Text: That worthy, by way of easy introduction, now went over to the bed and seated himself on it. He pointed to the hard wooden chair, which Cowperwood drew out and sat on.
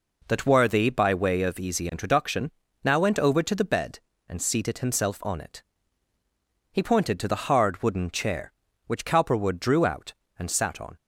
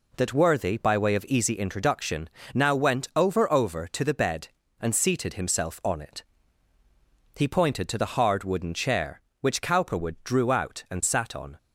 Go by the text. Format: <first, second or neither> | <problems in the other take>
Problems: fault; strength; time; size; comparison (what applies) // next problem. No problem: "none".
first | says "over" twice; at 3.5 s